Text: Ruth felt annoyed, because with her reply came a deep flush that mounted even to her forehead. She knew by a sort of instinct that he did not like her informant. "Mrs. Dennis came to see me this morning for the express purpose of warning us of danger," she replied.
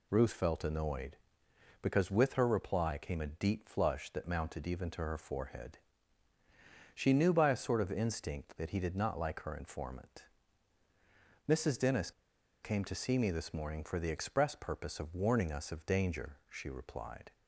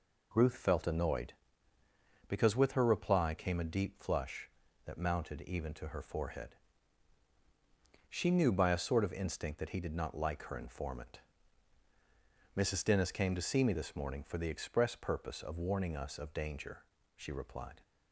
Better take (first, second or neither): second